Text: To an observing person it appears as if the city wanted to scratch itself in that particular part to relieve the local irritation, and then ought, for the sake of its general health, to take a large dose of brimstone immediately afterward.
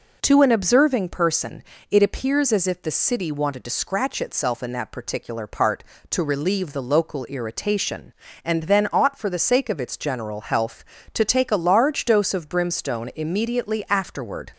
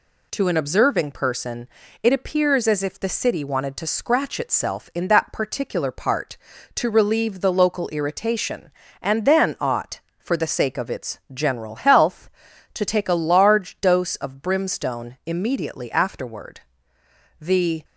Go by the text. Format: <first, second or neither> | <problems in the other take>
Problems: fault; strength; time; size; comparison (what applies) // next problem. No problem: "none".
first | pauses between "person" and "it"; slight; at 1.6 s; 0.36 s long; slight in the first // goes on to say "The"; slight; from 17.3 s on; 0.44 s long